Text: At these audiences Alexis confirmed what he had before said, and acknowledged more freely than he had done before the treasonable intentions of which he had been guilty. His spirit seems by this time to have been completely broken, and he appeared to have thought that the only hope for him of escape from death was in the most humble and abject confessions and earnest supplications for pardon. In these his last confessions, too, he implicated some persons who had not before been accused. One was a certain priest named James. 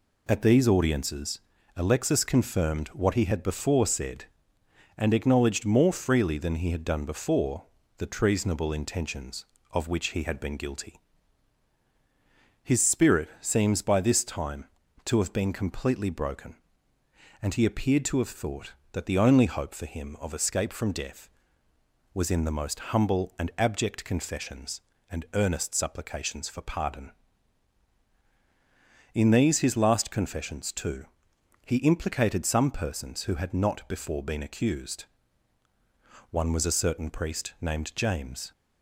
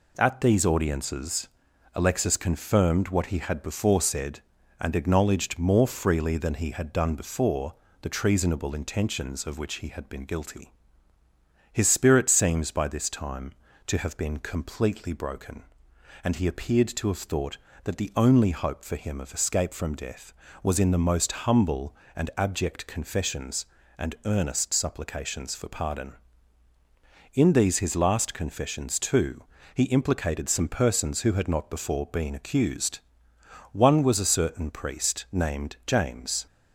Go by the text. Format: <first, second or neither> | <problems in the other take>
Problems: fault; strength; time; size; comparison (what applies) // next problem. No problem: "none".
neither | pauses between "audiences" and "Alexis"; the same in both // pauses between "before" and "the"; slight; the same in both